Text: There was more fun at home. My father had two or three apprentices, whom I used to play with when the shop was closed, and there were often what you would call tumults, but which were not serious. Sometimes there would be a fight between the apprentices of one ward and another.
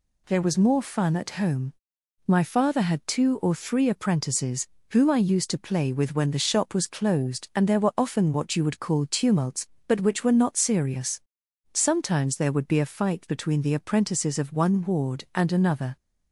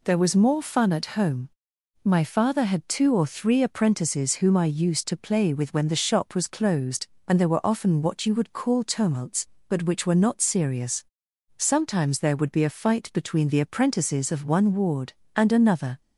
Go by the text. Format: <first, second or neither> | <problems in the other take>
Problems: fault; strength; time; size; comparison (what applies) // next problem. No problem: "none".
neither | none